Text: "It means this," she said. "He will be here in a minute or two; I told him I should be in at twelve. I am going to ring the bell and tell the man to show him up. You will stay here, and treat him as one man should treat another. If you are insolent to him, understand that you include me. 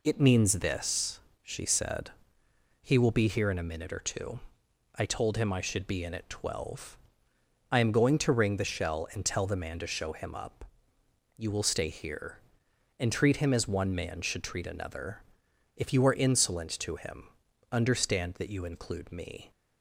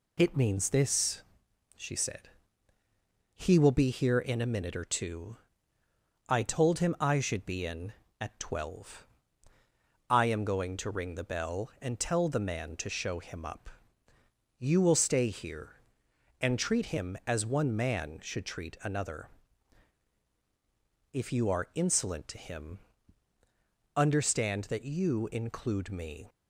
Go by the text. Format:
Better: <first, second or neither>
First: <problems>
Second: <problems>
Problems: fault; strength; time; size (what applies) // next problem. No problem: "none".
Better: second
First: says "shell" for "bell"; at 8.6 s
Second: none